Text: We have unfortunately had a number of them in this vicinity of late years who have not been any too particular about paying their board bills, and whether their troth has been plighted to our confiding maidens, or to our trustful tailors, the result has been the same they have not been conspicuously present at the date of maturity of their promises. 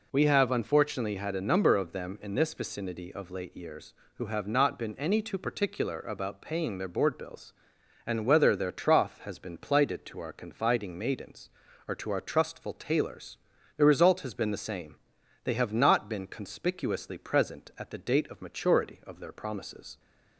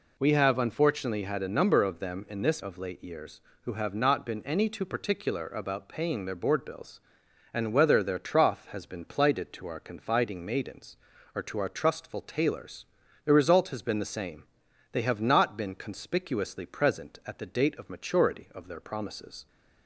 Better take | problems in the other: first | skips "vicinity"; at 2.6 s // pauses between "same" and "they"; noticeable; at 14.4 s; 0.50 s long; noticeable in the first

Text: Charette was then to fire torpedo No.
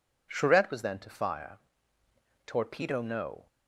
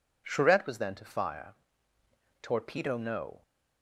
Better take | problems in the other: neither | pauses between "fire" and "torpedo"; noticeable; the same in both

